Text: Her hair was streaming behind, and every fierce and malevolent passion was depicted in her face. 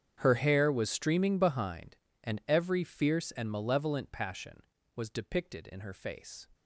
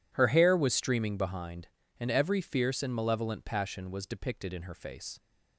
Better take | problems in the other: second | gets quieter; strong; throughout; 21.5 dB

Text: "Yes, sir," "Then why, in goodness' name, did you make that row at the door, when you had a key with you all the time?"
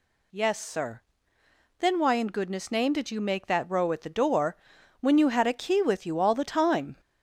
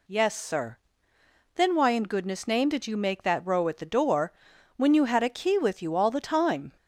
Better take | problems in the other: second | gets louder; noticeable; throughout; 4 dB

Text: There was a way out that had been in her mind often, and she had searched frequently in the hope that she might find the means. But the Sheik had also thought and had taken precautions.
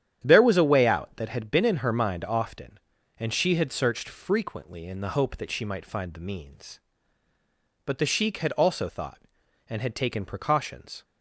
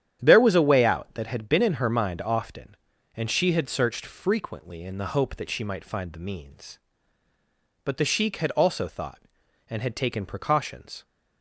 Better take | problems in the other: neither | starts louder than the rest; strong; the same in both

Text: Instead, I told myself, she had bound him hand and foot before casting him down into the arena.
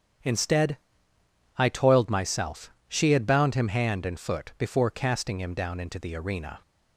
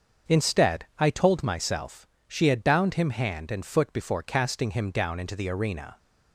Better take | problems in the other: second | starts louder than the rest; strong; until 2.0 s; 8.5 dB; also in the second // says "toiled" for "told"; at 1.6 s

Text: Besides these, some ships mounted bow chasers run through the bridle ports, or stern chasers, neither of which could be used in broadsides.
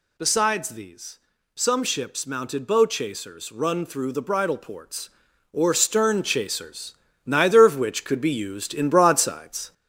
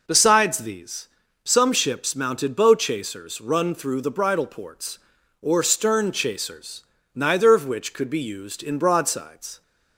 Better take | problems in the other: second | gets louder; slight; throughout; 3.5 dB

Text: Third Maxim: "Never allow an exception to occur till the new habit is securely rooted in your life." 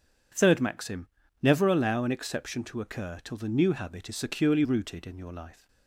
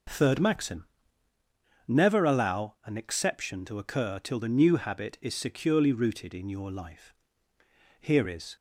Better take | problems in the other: first | goes on to say "Here is"; from 8.0 s on; 0.55 s long

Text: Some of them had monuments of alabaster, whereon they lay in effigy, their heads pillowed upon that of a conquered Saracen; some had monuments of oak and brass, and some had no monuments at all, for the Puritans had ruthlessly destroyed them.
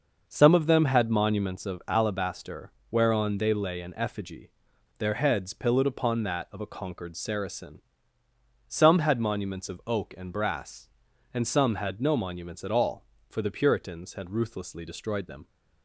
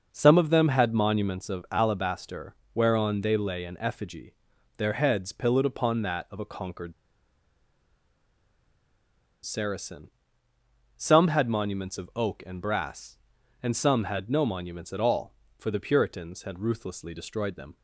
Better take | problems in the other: first | starts louder than the rest; noticeable; until 1.1 s; 6 dB; noticeable in the first // pauses between "conquered" and "Saracen"; strong; at 6.9 s; 2.5 s long

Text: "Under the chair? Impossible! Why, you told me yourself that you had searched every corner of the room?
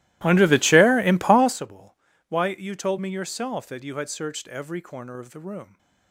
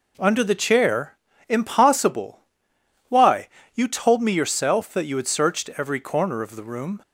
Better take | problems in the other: second | starts louder than the rest; strong; until 1.6 s; 17 dB

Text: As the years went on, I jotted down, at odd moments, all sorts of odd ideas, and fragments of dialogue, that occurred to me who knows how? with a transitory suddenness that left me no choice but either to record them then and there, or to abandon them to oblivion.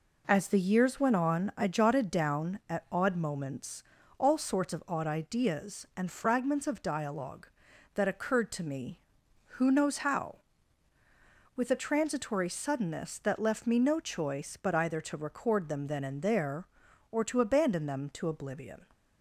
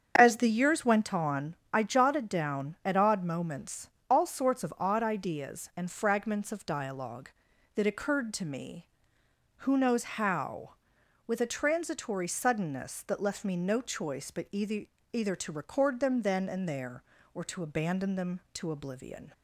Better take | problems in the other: first | starts louder than the rest; strong; until 1.1 s; 7 dB // says "either" twice; at 15.1 s

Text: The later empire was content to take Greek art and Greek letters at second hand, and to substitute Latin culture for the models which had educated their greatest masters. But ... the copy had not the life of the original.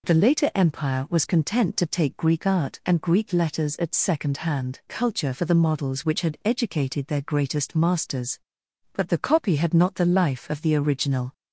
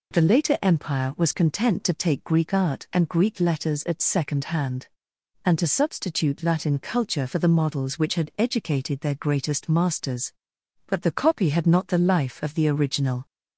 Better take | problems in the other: second | skips "and to substitute Latin"; at 4.8 s

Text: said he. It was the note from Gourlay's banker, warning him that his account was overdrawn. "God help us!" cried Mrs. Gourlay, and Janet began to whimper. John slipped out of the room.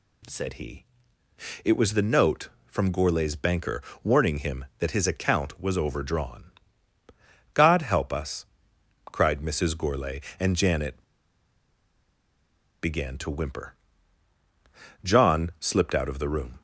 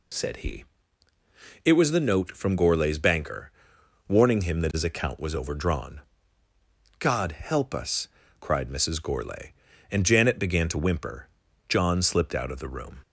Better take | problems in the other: second | pauses between "Janet" and "began"; strong; at 11.0 s; 1.7 s long

